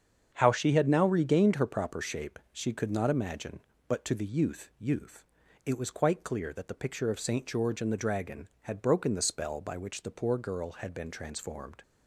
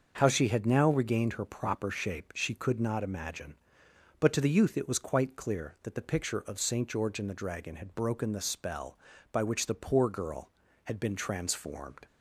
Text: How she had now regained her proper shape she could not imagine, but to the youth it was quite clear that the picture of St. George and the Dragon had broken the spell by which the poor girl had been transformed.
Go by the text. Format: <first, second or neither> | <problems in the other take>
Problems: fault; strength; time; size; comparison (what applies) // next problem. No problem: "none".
second | starts louder than the rest; strong; until 1.3 s; 7.5 dB; also in the second // says "youth" twice; at 4.7 s